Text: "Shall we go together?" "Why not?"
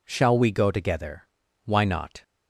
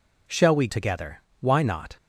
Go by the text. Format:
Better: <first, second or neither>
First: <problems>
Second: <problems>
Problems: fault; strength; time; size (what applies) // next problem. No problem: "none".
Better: first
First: none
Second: skips "go"; at 0.6 s